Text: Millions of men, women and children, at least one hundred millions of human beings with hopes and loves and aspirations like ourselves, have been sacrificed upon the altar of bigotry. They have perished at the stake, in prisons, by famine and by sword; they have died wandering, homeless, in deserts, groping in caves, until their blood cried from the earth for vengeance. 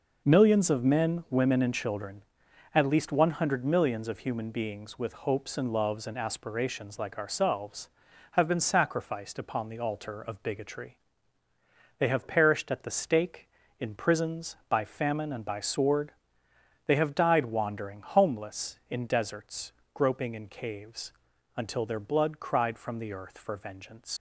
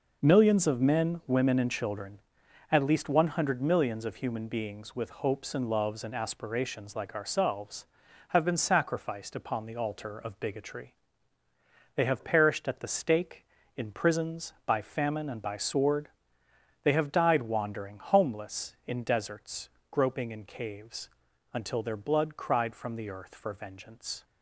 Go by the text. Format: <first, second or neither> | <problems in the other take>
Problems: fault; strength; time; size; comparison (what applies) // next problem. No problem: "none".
second | leaves "vengeance" unfinished; at 24.1 s; 105 ms